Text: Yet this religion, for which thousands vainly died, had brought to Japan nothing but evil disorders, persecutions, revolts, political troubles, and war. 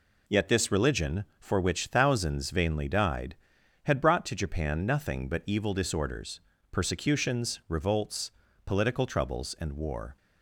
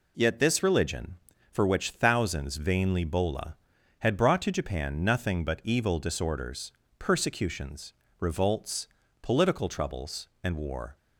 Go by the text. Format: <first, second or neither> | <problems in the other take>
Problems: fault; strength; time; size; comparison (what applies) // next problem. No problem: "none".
first | says "bola" for "died"; at 3.0 s